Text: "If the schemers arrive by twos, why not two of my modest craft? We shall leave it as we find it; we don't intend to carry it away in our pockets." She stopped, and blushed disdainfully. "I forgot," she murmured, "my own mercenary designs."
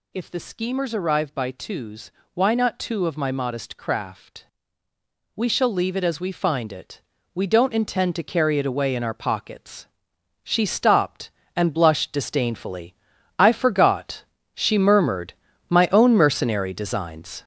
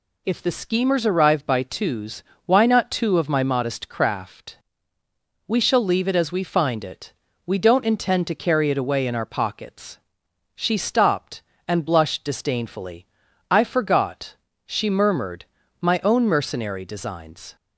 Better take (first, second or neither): second